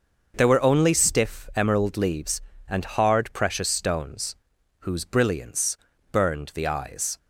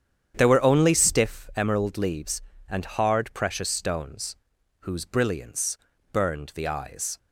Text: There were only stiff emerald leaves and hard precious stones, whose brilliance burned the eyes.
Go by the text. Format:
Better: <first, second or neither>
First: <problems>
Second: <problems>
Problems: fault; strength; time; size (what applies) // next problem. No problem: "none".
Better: first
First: pauses between "brilliance" and "burned"; slight; at 5.7 s; 0.34 s long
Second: starts louder than the rest; strong; until 1.4 s; 9 dB // pauses between "brilliance" and "burned"; slight; at 5.7 s; 0.34 s long